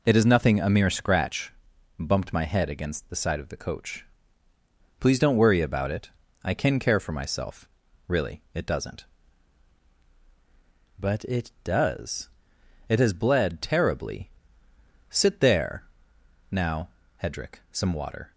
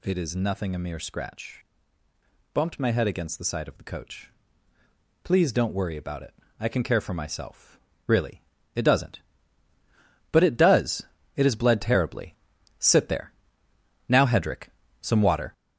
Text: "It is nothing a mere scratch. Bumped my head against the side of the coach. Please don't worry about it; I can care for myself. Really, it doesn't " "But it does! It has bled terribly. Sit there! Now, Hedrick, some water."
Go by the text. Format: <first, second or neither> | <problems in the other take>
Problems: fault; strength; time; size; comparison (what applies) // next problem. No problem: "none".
first | gets louder; slight; throughout; 3 dB